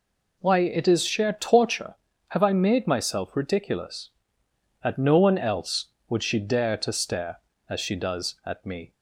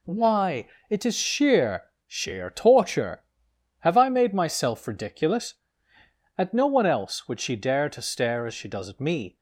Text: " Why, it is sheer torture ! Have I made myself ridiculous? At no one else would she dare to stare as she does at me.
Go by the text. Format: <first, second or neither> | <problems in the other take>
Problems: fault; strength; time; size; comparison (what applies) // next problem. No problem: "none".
first | says "sheer" twice; at 2.0 s